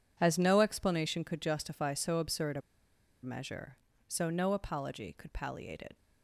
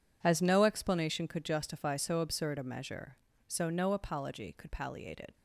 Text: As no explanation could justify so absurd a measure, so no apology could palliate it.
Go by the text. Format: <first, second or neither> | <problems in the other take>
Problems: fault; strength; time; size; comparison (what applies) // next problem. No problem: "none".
second | pauses between "a" and "measure"; noticeable; at 2.6 s; 0.62 s long